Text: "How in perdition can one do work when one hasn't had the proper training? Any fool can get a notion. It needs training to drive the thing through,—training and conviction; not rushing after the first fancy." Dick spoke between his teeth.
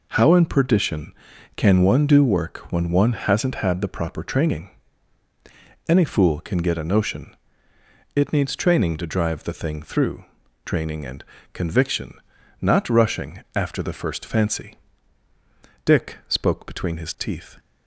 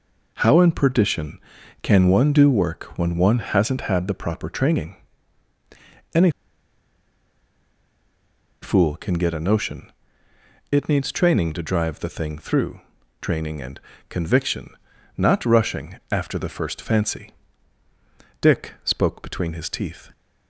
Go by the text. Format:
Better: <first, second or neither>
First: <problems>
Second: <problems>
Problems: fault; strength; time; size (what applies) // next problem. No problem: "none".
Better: first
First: pauses between "and" and "conviction"; slight; at 11.2 s; 0.30 s long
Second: pauses between "Any" and "fool"; strong; at 6.2 s; 2.3 s long // pauses between "and" and "conviction"; slight; at 13.7 s; 0.30 s long